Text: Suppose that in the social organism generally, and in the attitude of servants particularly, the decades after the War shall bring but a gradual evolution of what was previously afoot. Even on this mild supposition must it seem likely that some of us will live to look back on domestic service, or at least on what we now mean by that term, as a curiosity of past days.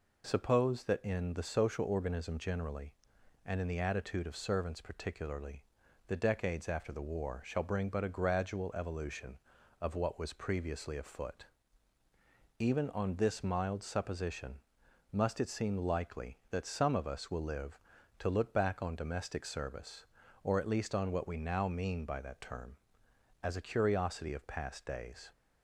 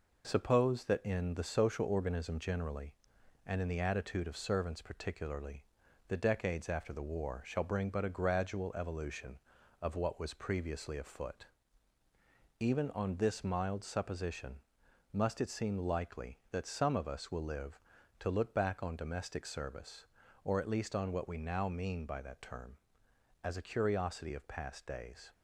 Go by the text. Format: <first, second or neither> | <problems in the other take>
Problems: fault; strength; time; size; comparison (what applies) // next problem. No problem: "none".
first | gets quieter; throughout; 4 dB // pauses between "supposition" and "must"; noticeable; at 14.5 s; 0.56 s long; noticeable in the first